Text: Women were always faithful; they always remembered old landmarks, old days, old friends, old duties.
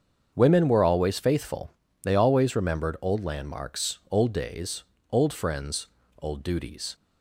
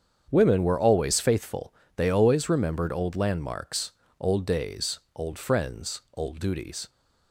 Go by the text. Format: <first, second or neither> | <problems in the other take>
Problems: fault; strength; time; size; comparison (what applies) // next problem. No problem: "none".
neither | starts louder than the rest; strong; the same in both